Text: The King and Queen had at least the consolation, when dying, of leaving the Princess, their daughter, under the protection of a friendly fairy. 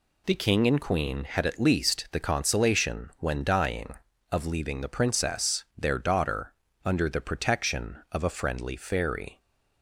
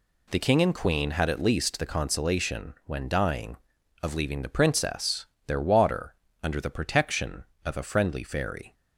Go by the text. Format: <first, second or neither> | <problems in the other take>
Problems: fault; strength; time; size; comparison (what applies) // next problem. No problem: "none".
first | says "water" for "daughter"; at 5.5 s